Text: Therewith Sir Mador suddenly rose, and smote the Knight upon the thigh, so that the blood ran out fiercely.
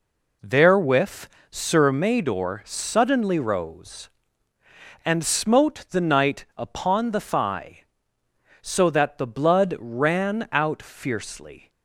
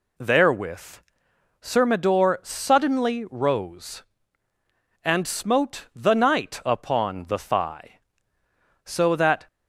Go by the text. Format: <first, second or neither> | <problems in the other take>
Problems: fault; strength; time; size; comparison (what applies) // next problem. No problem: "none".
first | pauses between "Therewith" and "Sir"; noticeable; at 1.0 s; 0.60 s long; slight in the first // stops before "the blood ran out fiercely"; at 9.4 s